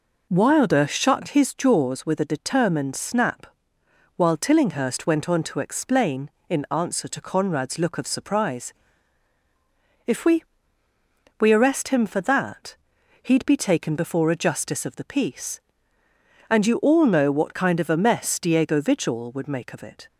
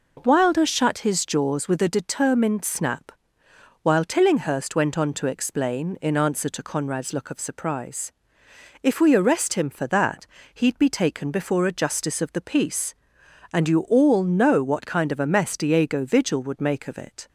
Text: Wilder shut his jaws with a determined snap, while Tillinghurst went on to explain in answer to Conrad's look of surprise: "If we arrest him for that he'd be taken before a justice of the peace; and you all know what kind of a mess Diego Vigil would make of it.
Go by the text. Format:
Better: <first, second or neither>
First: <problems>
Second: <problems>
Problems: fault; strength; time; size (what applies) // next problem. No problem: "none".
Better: second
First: says "we" twice; at 11.3 s // pauses between "that" and "he'd"; noticeable; at 12.7 s; 0.46 s long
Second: pauses between "that" and "he'd"; slight; at 10.2 s; 0.28 s long